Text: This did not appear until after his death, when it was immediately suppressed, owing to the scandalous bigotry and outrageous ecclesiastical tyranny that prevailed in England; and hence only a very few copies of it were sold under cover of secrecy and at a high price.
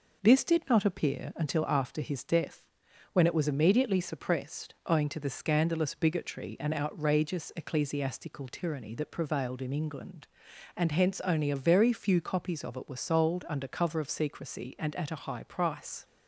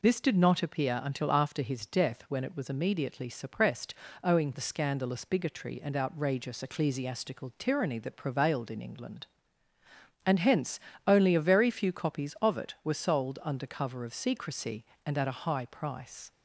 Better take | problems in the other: first | skips "to"; at 4.5 s // pauses between "hence" and "only"; slight; at 10.7 s; 0.26 s long

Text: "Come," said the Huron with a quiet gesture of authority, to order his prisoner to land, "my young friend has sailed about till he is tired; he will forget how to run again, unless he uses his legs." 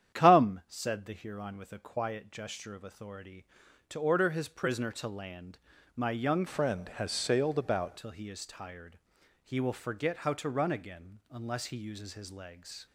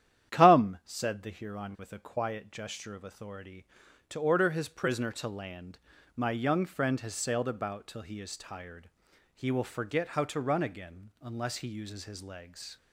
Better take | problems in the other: second | starts louder than the rest; strong; until 1.2 s; 9.5 dB; strong in the second // changes voice from "friend" to "about"; from 6.4 to 7.9 s; 1.5 s long

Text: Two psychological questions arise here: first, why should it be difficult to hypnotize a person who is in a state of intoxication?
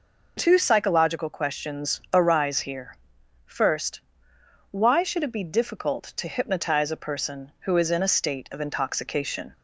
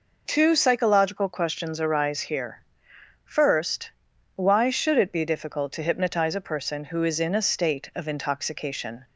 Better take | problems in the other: neither | none

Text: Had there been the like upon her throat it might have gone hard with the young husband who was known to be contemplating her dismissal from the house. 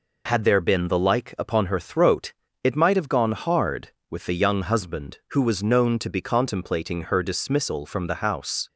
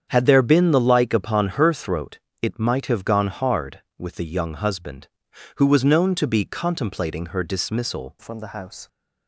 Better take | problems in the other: first | starts louder than the rest; strong; until 1.1 s; 8 dB // pauses between "throat" and "it"; slight; at 2.1 s; 0.22 s long; slight in the first // changes voice at "from"; from 8.1 s on; 0.7 s long

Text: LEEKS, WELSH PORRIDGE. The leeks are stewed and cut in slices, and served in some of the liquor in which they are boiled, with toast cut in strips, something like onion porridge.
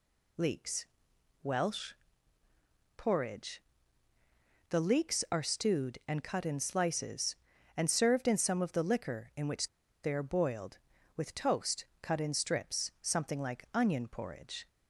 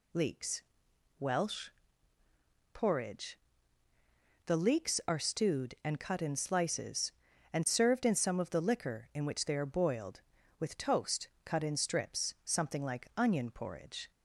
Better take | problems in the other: second | pauses between "WELSH" and "PORRIDGE"; at 1.9 s; 1.0 s long; also in the second // pauses between "which" and "they"; slight; at 9.6 s; 0.35 s long // pauses between "toast" and "cut"; slight; at 11.8 s; 0.16 s long; slight in the second

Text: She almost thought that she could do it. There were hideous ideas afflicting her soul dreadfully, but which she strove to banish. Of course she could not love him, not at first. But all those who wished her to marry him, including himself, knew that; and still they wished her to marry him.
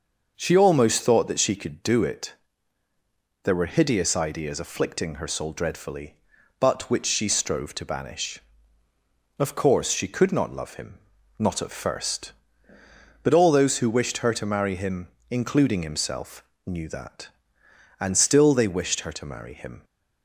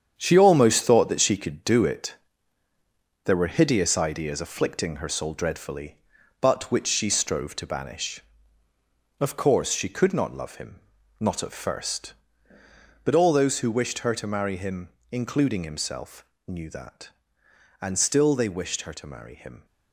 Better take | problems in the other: first | gets quieter; strong; throughout; 8.5 dB // starts louder than the rest; strong; until 1.1 s; 8 dB; noticeable in the first

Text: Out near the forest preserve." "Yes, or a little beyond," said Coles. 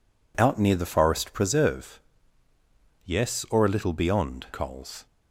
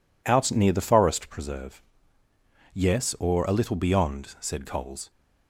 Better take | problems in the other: second | skips "said"; at 4.5 s

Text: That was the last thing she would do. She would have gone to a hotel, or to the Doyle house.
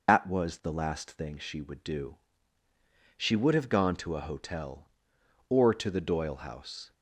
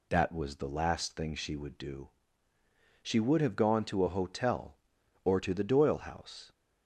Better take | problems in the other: second | loses the start of "That"; at 0.0 s; 85 ms

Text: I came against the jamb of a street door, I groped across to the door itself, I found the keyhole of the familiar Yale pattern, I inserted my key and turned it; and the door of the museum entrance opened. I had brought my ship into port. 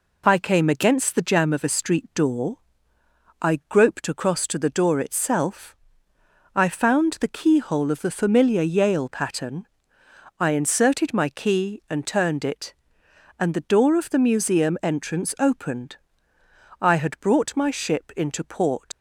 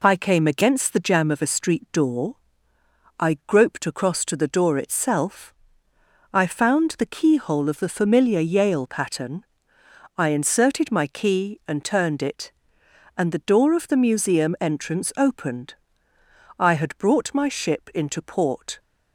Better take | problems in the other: second | leaves "port" unfinished; at 18.9 s; 105 ms

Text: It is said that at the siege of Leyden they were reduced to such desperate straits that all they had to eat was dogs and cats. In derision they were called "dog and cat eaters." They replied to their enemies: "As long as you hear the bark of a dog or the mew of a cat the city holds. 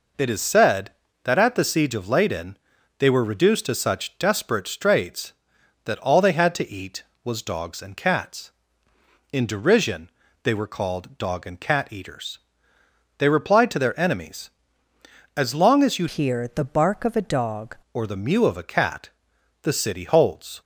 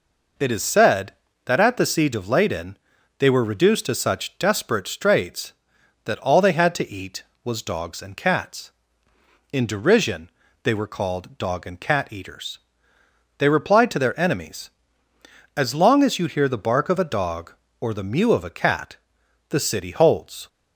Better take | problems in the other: second | pauses between "Leyden" and "they"; at 2.5 s; 0.42 s long; also in the second // pauses between "derision" and "they"; slight; at 10.0 s; 0.36 s long; slight in the second // changes voice from "hear" to "dog"; from 16.0 to 17.7 s; 1.7 s long // pauses between "cat" and "the"; noticeable; at 19.0 s; 0.54 s long; noticeable in the second

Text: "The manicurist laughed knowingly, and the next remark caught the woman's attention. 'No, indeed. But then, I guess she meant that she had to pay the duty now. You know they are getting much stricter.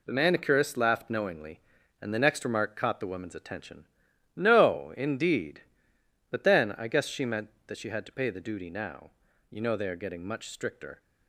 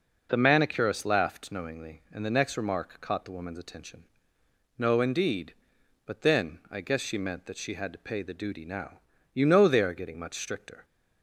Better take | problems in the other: second | gets quieter; strong; throughout; 7 dB

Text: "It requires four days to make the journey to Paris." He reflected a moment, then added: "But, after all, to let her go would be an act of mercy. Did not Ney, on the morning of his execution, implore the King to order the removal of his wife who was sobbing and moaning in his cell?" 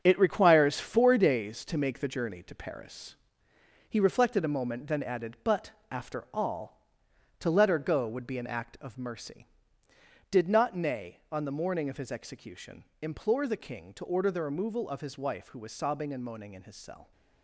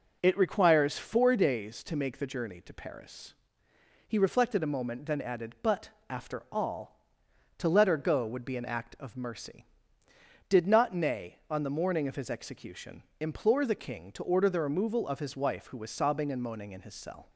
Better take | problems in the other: second | gets quieter; strong; throughout; 8 dB

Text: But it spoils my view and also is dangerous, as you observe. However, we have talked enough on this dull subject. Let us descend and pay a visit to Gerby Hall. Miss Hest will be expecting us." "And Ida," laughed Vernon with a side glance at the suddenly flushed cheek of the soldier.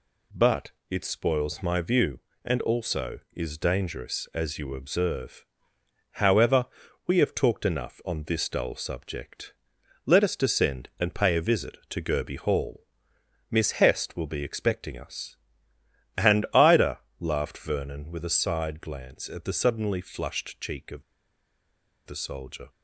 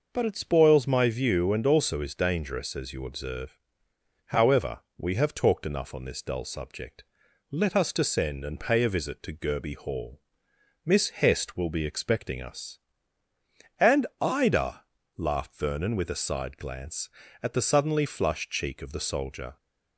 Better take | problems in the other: second | pauses between "But" and "it"; slight; at 0.7 s; 0.18 s long // pauses between "of" and "the"; at 21.0 s; 1.0 s long

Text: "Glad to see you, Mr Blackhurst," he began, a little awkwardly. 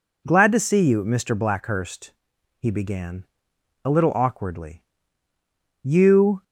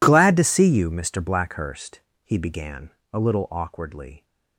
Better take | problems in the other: second | goes on to say "You"; from 5.8 s on; 0.60 s long

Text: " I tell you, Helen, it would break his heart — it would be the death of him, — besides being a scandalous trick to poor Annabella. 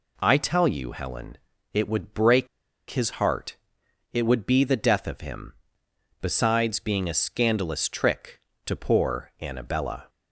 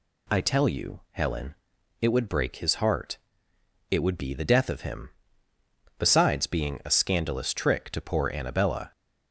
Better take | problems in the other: second | pauses between "break" and "his"; at 2.4 s; 0.43 s long

